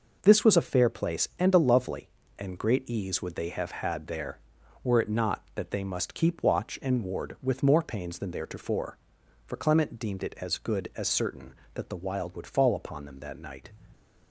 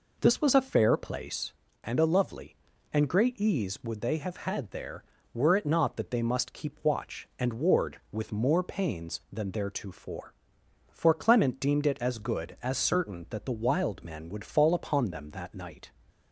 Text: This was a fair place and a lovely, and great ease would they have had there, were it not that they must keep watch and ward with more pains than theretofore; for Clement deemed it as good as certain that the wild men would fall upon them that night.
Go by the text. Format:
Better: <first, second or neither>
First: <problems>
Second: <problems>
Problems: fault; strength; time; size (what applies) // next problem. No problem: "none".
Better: second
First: skips "men"; at 12.3 s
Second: none